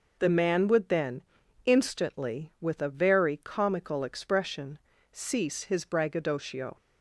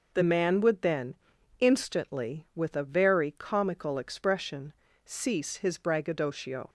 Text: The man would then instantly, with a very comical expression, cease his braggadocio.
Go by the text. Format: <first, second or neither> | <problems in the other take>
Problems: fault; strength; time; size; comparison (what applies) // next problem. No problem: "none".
neither | pauses between "then" and "instantly"; the same in both